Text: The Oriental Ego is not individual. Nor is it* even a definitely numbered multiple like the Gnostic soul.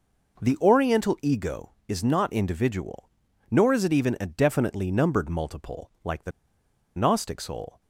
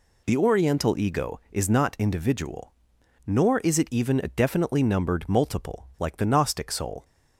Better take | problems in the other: second | pauses between "the" and "Gnostic"; noticeable; at 6.3 s; 0.65 s long

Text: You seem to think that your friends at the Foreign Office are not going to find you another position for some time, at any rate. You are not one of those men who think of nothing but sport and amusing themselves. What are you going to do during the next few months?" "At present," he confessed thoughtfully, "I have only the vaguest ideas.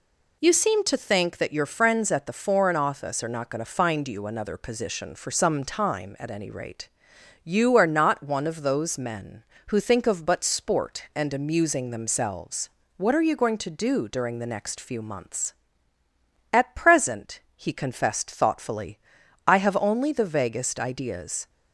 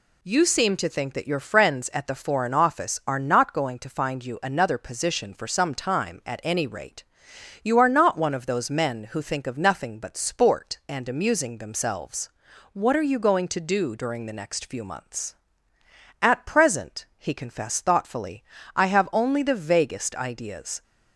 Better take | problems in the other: second | skips "nothing"; at 10.2 s

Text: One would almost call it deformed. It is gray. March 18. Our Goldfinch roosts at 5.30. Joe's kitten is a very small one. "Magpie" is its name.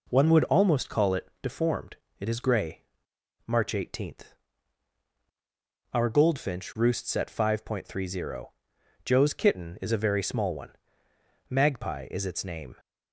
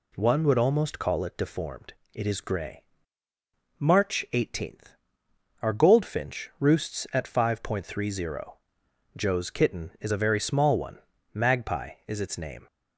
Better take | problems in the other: neither | none

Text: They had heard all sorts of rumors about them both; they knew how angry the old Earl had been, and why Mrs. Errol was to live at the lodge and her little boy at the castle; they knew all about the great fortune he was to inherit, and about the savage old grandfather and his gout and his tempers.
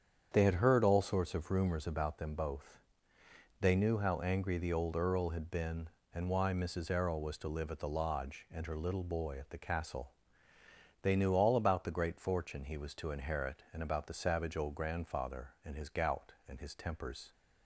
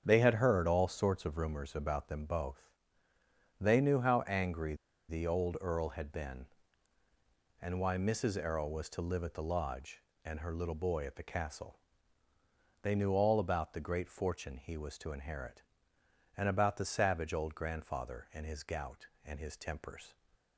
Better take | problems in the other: first | starts louder than the rest; strong; until 1.0 s; 8 dB; strong in the first // pauses between "angry" and "the"; slight; at 4.7 s; 0.34 s long

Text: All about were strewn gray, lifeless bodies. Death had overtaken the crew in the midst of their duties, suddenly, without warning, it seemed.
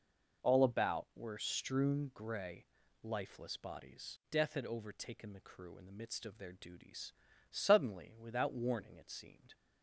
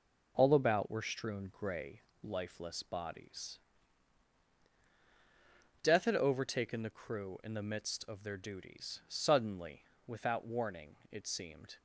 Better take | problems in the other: neither | none

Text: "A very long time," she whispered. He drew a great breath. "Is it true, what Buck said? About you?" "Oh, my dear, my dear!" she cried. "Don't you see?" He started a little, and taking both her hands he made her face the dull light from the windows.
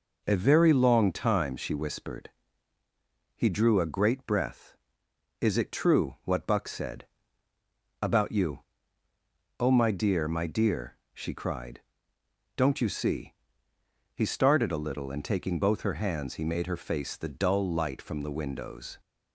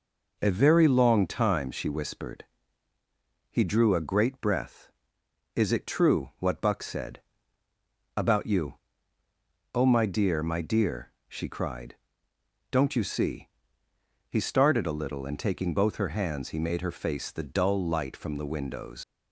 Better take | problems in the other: first | leaves "windows" unfinished; at 19.0 s; 110 ms

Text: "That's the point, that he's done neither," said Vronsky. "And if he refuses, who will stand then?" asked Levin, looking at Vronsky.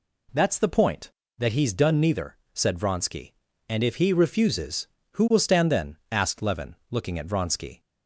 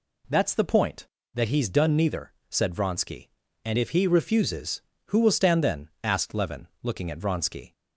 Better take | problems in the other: neither | none

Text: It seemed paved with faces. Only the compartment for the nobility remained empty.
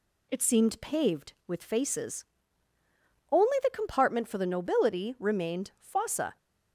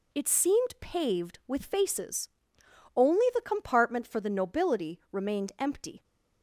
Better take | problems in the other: second | says "fossa" for "empty"; at 5.8 s

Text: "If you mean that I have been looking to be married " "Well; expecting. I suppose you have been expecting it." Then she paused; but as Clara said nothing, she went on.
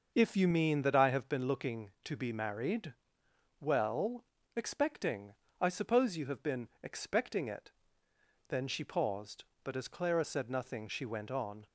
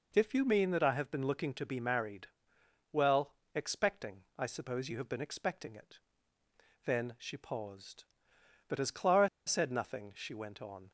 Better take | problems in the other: first | pauses between "Clara" and "said"; slight; at 9.2 s; 0.18 s long

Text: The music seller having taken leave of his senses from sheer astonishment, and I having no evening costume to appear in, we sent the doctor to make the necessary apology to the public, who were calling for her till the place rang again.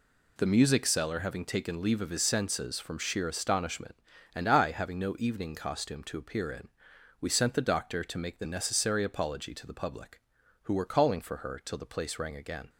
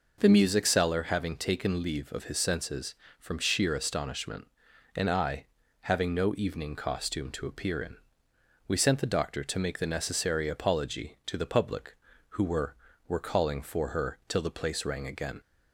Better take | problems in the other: first | pauses between "I" and "having"; at 5.4 s; 0.38 s long // says "were" twice; at 13.0 s

